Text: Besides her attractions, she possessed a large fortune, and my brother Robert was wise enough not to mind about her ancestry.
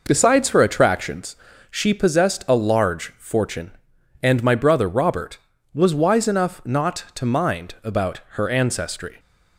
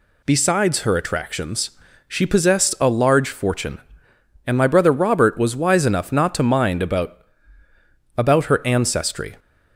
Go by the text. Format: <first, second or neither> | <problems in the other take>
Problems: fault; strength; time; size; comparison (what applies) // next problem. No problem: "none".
first | says "about" twice; at 8.1 s